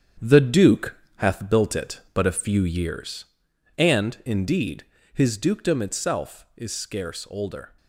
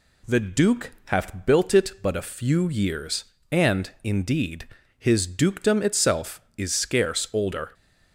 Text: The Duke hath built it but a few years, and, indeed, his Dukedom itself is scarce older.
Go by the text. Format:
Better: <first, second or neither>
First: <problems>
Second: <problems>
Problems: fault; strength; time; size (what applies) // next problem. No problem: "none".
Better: second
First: gets quieter; strong; throughout; 7.5 dB // pauses between "Duke" and "hath"; slight; at 0.9 s; 0.20 s long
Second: none